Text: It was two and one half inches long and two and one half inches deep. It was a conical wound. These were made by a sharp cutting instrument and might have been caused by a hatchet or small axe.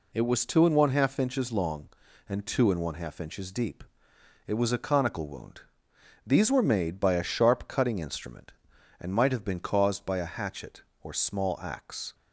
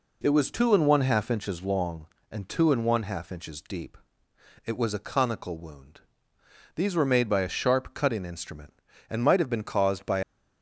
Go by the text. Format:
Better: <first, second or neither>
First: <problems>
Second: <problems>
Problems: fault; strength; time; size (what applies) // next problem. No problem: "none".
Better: first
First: none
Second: stops before "a hatchet or small axe"; at 10.2 s